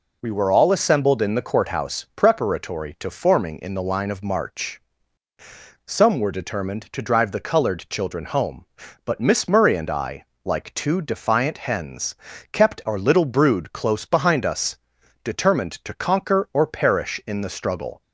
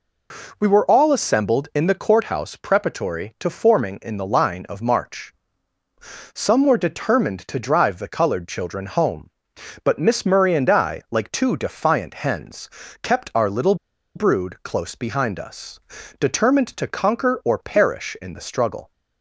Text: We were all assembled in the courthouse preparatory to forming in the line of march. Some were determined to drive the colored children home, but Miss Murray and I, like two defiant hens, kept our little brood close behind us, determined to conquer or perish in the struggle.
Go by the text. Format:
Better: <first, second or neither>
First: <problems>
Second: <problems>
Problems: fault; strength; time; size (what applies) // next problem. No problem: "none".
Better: first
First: none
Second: pauses between "little" and "brood"; at 13.7 s; 0.40 s long